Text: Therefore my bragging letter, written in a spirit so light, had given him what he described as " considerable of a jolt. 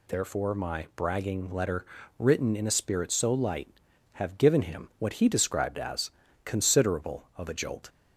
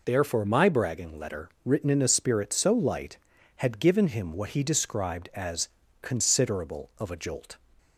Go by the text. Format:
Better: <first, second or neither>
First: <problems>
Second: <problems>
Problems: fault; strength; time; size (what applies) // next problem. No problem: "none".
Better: second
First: says "have" for "had"; at 4.1 s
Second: none